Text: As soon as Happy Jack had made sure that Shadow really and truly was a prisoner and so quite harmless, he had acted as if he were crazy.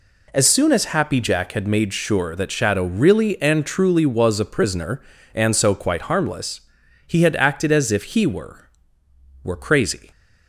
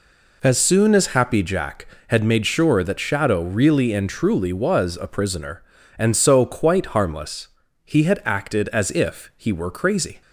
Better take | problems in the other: second | says "were" twice; at 9.4 s

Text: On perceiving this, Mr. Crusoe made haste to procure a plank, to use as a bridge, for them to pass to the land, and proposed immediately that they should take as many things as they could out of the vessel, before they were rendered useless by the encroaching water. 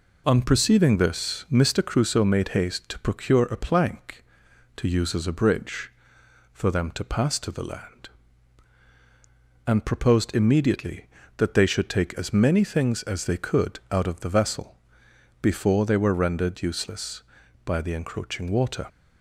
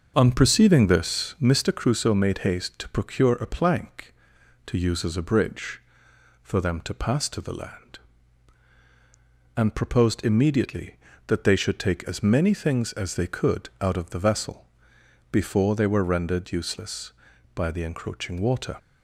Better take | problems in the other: first | starts louder than the rest; until 1.4 s; 6.5 dB

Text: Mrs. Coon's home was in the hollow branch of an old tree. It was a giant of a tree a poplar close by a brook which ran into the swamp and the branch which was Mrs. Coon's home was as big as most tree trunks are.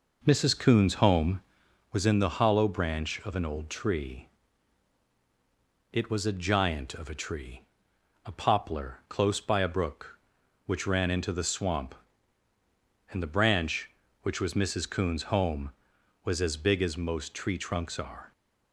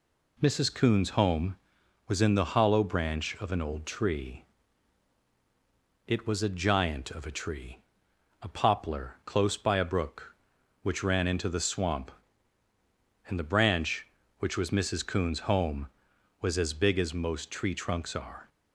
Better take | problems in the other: second | starts louder than the rest; noticeable; until 2.0 s; 5 dB // pauses between "tree" and "a"; noticeable; at 7.6 s; 0.64 s long; noticeable in the second

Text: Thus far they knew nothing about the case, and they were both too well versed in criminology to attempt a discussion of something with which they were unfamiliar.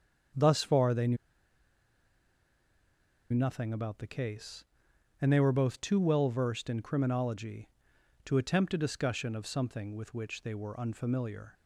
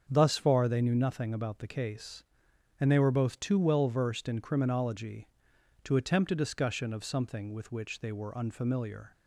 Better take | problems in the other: second | starts louder than the rest; until 3.5 s; 7 dB; also in the second // pauses between "knew" and "nothing"; strong; at 1.1 s; 2.1 s long

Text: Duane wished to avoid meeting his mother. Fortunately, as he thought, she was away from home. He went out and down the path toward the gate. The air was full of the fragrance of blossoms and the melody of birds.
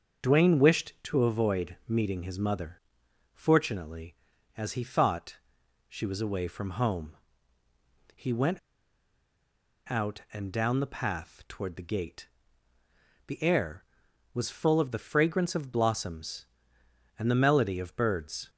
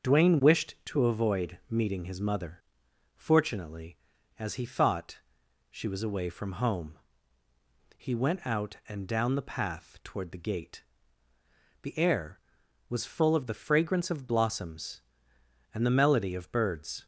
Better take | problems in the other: second | starts louder than the rest; until 1.3 s; 7 dB; also in the second // pauses between "went" and "out"; strong; at 8.5 s; 1.3 s long

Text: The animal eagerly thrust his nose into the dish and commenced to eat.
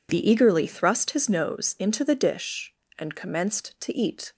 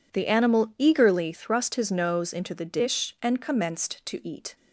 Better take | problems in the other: second | skips "animal"; at 0.2 s

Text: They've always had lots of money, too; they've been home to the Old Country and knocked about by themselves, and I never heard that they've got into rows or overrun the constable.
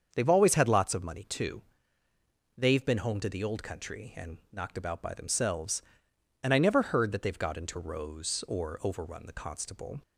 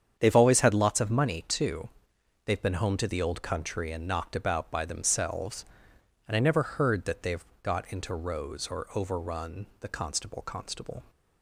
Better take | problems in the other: first | starts louder than the rest; strong; until 1.1 s; 8 dB; strong in the first // pauses between "they've" and "got"; slight; at 7.4 s; 0.16 s long // says "constable" twice; at 10.4 s

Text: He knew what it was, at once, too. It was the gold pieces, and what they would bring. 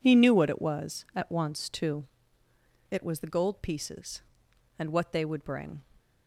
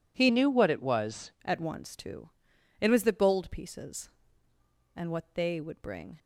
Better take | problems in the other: first | changes voice from "knew" to "was"; from 0.2 to 1.3 s; 1.1 s long

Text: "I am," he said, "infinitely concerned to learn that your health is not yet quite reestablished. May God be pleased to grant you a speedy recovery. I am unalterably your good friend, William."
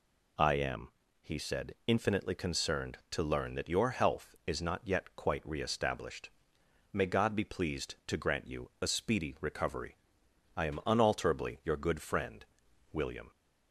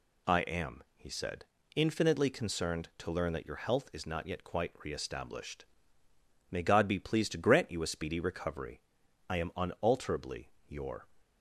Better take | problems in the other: first | pauses between "unalterably" and "your"; slight; at 10.4 s; 0.18 s long // stops before "good friend William"; at 11.1 s

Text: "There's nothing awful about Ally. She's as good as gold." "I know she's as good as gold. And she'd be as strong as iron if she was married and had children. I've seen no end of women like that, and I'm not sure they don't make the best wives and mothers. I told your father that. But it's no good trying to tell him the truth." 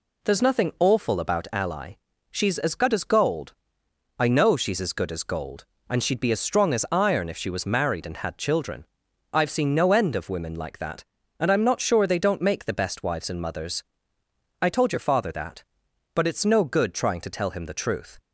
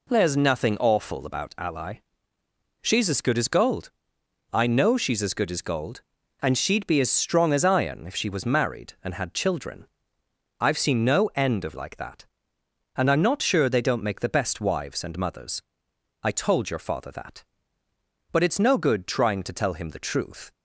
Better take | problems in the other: first | skips "women"; at 11.7 s

